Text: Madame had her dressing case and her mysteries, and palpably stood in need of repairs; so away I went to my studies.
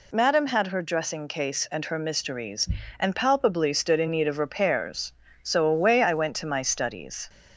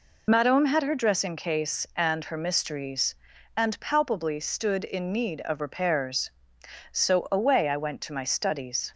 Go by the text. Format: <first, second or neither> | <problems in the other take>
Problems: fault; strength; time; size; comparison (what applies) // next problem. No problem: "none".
first | loses the start of "Madame"; at 0.2 s; 25 ms